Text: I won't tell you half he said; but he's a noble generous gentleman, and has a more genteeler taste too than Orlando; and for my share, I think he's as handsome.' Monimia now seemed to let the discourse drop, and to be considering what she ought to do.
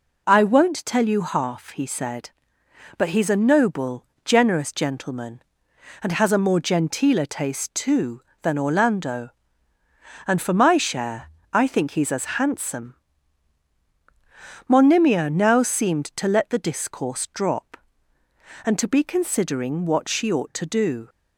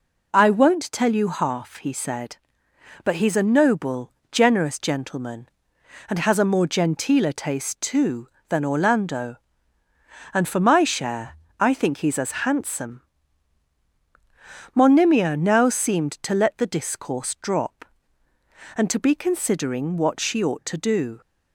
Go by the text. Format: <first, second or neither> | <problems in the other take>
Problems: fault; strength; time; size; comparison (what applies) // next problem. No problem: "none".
neither | pauses between "noble" and "generous"; slight; the same in both